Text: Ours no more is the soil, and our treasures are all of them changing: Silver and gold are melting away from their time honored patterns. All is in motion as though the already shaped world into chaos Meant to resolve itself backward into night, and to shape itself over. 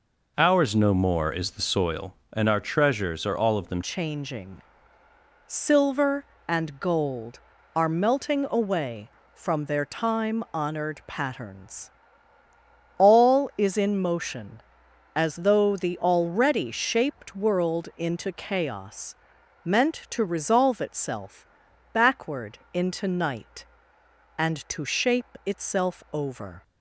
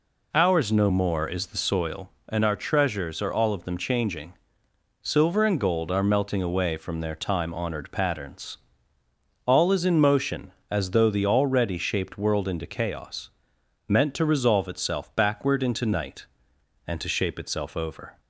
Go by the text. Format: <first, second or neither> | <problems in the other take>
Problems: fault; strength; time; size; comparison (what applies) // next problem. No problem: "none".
second | changes voice at "changing"; from 3.8 s on; 22.8 s long // pauses between "chaos" and "Meant"; noticeable; at 19.1 s; 0.50 s long; noticeable in the second // pauses between "itself" and "backward"; noticeable; at 21.4 s; 0.48 s long // pauses between "backward" and "into"; slight; at 22.5 s; 0.16 s long